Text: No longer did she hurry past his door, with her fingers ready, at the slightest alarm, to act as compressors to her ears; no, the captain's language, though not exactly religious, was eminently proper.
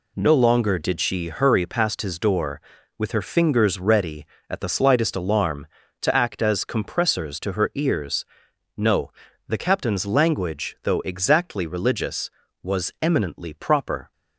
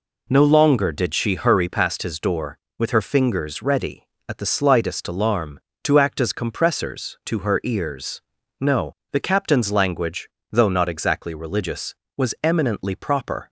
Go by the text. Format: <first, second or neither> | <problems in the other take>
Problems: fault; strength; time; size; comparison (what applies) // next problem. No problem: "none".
second | skips "not"; at 10.9 s